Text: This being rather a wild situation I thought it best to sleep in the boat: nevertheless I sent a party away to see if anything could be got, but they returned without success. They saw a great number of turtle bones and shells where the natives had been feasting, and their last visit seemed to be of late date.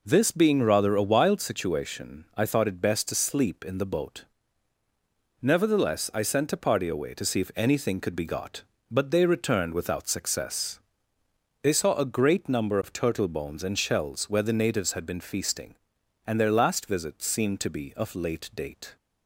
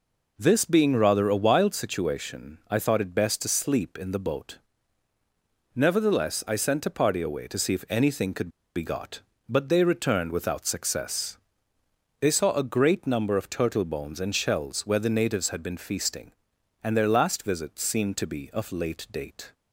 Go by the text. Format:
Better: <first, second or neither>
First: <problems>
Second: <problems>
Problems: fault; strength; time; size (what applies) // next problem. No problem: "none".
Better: first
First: none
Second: pauses between "could" and "be"; slight; at 8.4 s; 0.27 s long